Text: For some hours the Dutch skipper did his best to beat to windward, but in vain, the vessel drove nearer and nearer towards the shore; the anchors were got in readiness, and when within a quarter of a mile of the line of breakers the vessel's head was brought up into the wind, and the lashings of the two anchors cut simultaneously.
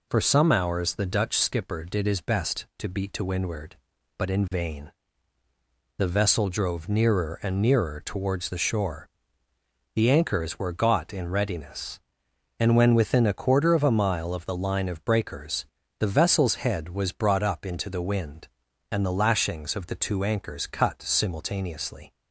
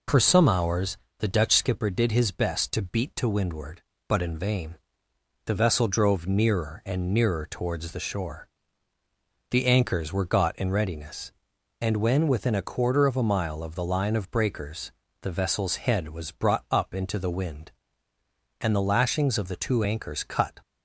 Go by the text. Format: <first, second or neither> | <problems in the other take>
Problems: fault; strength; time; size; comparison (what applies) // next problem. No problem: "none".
first | pauses between "hours" and "the"; slight; at 0.9 s; 0.22 s long // pauses between "breakers" and "the"; slight; at 14.9 s; 0.30 s long; slight in the first // stops before "simultaneously"; at 20.6 s